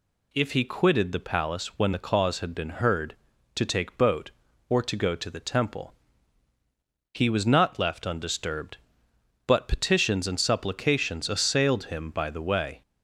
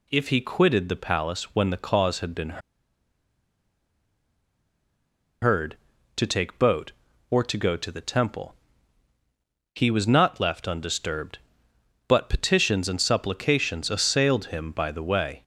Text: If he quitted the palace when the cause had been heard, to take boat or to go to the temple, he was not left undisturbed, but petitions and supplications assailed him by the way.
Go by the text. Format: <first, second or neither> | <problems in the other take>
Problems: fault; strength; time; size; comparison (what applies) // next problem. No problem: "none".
first | pauses between "been" and "heard"; strong; at 2.6 s; 2.8 s long